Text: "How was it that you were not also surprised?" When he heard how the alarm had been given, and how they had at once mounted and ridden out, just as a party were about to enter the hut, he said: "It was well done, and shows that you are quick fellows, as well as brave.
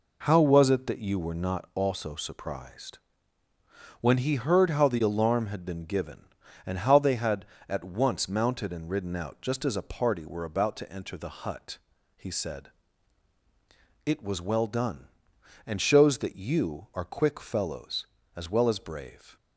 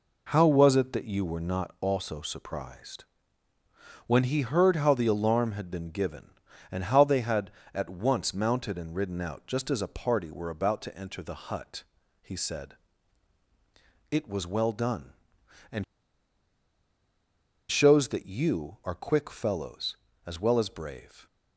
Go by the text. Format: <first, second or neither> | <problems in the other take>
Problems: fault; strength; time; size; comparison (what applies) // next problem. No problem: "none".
first | pauses between "and" and "shows"; strong; at 15.8 s; 1.8 s long